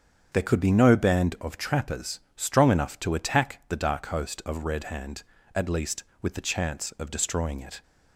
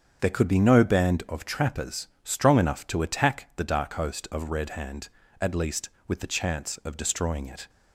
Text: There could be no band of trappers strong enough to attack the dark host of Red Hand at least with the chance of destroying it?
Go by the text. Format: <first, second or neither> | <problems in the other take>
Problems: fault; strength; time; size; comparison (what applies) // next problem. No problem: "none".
neither | starts louder than the rest; strong; the same in both // pauses between "trappers" and "strong"; slight; the same in both